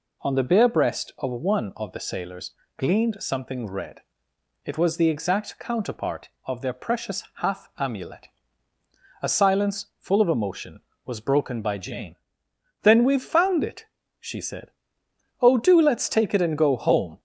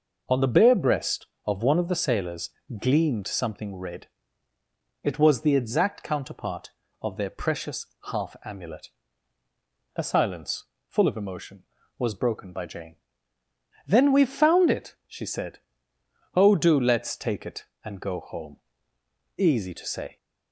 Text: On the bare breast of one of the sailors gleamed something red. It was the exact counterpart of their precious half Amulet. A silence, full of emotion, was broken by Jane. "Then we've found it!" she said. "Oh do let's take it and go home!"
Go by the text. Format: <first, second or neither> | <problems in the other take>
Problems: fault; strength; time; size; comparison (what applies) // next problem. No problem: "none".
first | pauses between "sailors" and "gleamed"; slight; at 2.4 s; 0.32 s long; slight in the first // pauses between "precious" and "half"; slight; at 7.8 s; 0.26 s long // goes on to say "Easy to say"; noticeable; from 19.3 s on; 0.80 s long